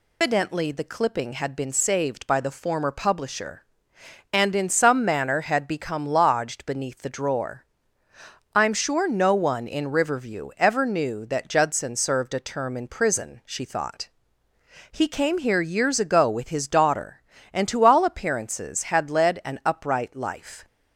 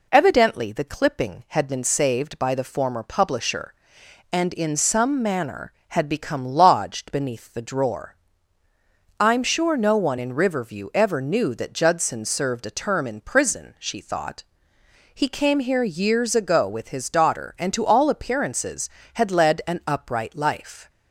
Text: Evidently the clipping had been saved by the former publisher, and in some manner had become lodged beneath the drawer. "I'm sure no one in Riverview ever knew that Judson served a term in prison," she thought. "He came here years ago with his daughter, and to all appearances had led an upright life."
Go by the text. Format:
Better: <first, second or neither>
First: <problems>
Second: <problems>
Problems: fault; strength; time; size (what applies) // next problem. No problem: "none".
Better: second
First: loses the start of "Evidently"; at 0.2 s; 135 ms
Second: none